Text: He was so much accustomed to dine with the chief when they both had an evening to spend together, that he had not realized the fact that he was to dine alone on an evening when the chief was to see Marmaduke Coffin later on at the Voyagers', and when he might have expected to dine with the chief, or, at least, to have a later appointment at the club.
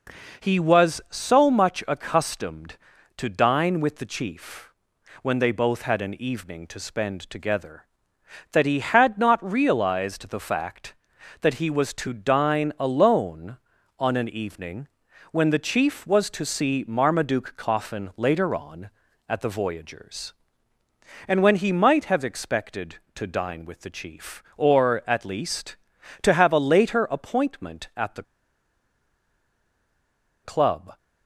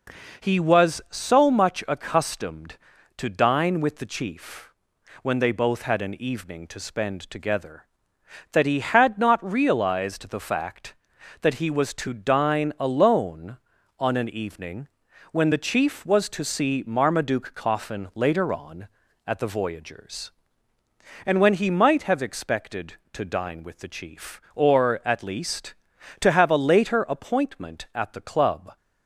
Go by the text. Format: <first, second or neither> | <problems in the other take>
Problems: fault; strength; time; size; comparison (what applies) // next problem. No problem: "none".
second | pauses between "chief" and "when"; noticeable; at 4.6 s; 0.52 s long; noticeable in the second // pauses between "evening" and "when"; noticeable; at 14.8 s; 0.46 s long; noticeable in the second // pauses between "the" and "club"; strong; at 28.2 s; 2.2 s long